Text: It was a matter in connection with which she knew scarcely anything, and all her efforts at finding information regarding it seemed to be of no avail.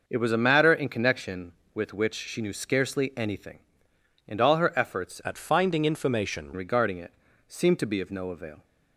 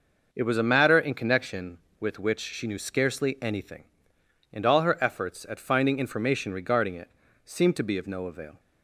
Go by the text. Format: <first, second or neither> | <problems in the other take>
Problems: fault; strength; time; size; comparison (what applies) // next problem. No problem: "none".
second | changes voice from "at" to "information"; from 5.2 to 6.5 s; 1.3 s long // pauses between "it" and "seemed"; slight; at 7.1 s; 0.36 s long; slight in the second